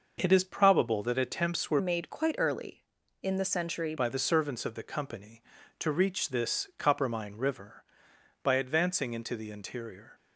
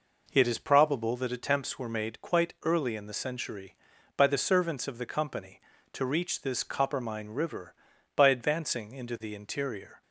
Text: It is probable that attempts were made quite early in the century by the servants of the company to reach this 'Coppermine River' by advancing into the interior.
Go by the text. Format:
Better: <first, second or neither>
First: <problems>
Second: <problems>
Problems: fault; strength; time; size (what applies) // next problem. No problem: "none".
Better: second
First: changes voice from "made" to "century"; from 1.7 to 3.9 s; 2.2 s long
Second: none